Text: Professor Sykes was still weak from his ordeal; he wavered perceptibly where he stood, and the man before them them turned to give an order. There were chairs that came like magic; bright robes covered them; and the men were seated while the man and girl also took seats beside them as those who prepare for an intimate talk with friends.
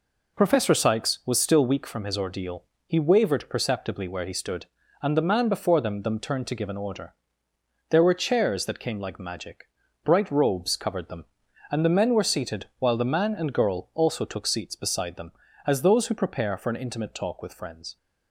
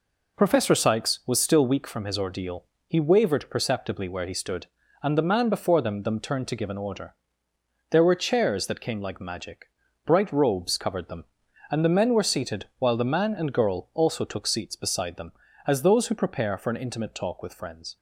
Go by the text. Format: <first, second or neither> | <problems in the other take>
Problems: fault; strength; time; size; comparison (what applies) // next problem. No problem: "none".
neither | none